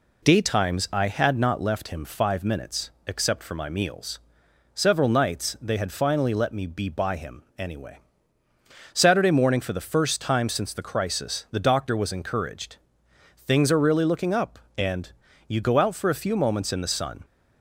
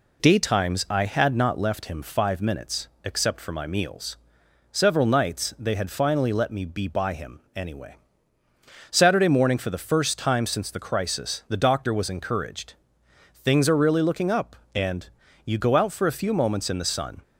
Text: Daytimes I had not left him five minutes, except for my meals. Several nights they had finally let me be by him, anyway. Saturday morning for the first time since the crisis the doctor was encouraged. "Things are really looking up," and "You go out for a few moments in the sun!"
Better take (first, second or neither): neither